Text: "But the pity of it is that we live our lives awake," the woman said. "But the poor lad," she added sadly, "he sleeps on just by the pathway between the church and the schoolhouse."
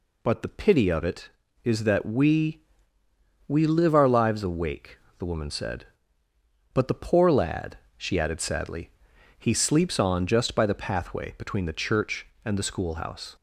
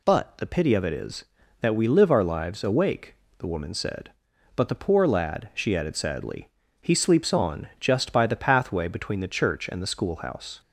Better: second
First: says "we" twice; at 3.4 s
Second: none

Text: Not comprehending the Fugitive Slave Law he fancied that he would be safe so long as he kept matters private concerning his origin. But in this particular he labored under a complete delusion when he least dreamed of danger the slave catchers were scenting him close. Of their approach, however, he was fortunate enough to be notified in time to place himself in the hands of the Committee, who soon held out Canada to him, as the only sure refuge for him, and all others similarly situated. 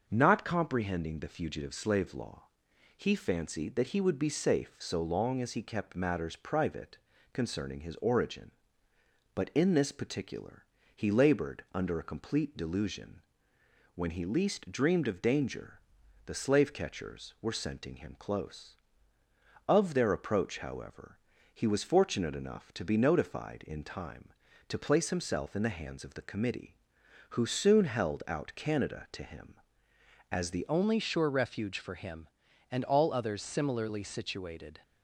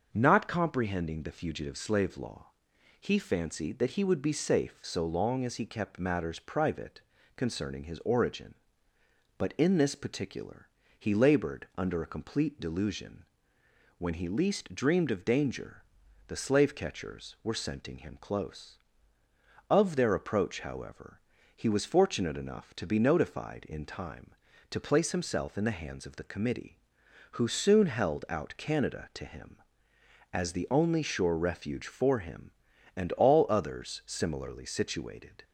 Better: second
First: starts louder than the rest; noticeable; until 1.1 s; 6 dB // pauses between "Law" and "he"; noticeable; at 2.4 s; 0.56 s long // pauses between "private" and "concerning"; slight; at 6.9 s; 0.34 s long // pauses between "particular" and "he"; slight; at 10.6 s; 0.32 s long // pauses between "delusion" and "when"; noticeable; at 13.1 s; 0.74 s long // pauses between "danger" and "the"; noticeable; at 15.7 s; 0.46 s long // changes voice at "only"; from 30.6 s on; 4.2 s long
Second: starts louder than the rest; noticeable; until 1.1 s; 6 dB // pauses between "Law" and "he"; noticeable; at 2.4 s; 0.56 s long // pauses between "private" and "concerning"; slight; at 7.0 s; 0.34 s long // pauses between "particular" and "he"; slight; at 10.6 s; 0.32 s long // pauses between "delusion" and "when"; noticeable; at 13.2 s; 0.74 s long // pauses between "danger" and "the"; at 15.8 s; 0.44 s long

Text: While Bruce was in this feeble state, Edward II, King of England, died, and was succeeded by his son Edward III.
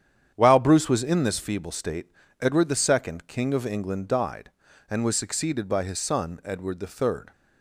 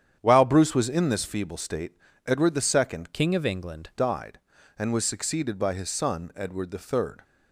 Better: first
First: starts louder than the rest; strong; until 1.3 s; 9 dB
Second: starts louder than the rest; strong; until 1.2 s; 9 dB // changes voice from "King" to "England"; from 3.1 to 3.8 s; 0.7 s long

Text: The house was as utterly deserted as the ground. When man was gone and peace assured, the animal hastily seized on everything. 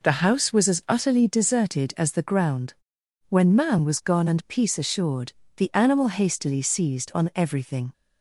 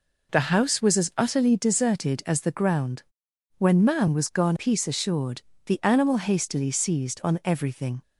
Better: first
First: none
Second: skips "and"; at 4.5 s

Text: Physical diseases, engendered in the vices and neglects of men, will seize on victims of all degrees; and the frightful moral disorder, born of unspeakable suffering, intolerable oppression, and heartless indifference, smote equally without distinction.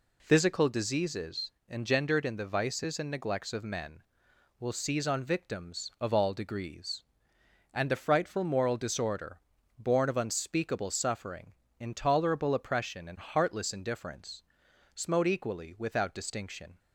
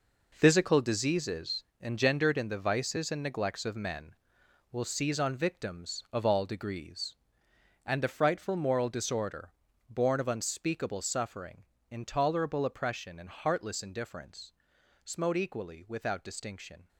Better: first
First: none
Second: gets quieter; strong; throughout; 10.5 dB

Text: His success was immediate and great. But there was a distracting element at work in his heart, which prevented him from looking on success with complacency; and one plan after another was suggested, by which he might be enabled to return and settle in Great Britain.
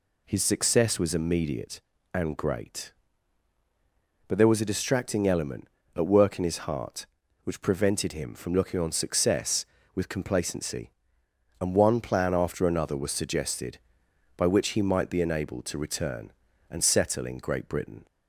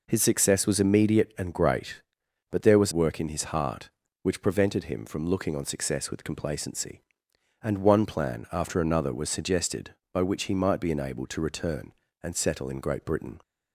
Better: first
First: none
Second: skips "a distracting element at"; at 2.9 s

